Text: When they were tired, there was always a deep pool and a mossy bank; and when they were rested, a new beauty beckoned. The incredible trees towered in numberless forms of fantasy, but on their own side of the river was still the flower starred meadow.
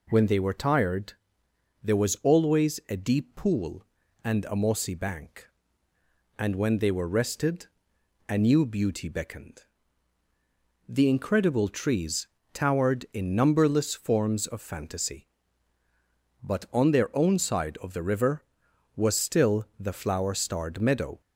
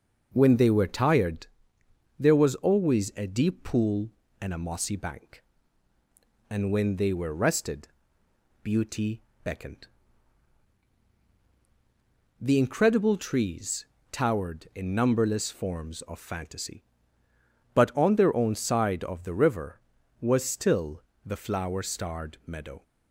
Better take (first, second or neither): first